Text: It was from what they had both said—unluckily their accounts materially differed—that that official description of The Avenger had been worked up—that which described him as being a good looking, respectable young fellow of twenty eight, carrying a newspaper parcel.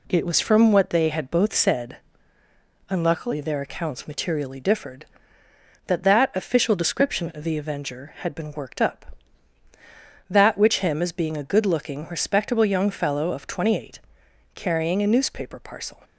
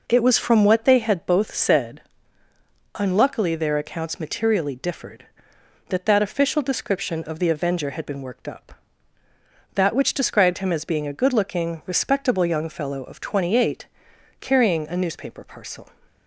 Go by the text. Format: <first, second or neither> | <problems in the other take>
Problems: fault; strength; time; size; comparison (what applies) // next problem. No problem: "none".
second | skips "described"; at 10.7 s